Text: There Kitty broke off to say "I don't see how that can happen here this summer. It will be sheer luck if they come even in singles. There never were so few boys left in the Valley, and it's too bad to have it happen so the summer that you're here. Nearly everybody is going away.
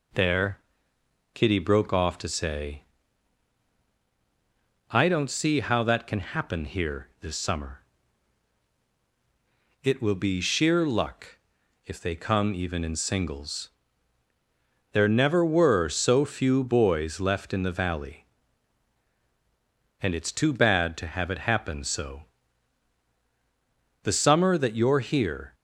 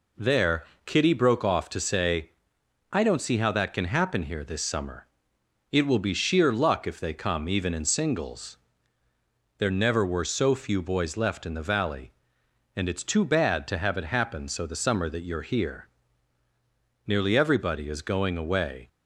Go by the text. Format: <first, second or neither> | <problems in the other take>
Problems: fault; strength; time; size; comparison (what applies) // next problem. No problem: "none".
second | pauses between "There" and "Kitty"; noticeable; at 0.5 s; 0.76 s long; slight in the second // pauses between "say" and "I"; strong; at 2.8 s; 2.0 s long; noticeable in the second // pauses between "luck" and "if"; noticeable; at 11.3 s; 0.48 s long // pauses between "so" and "the"; strong; at 22.2 s; 1.7 s long // stops before "Nearly everybody is going away"; at 25.5 s